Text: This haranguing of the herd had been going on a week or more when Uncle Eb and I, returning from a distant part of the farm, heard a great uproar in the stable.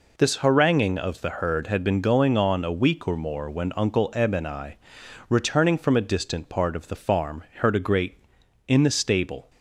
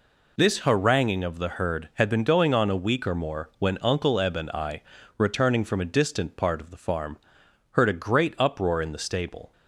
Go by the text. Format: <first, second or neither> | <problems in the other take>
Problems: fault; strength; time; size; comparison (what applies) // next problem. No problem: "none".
second | skips "uproar"; at 8.4 s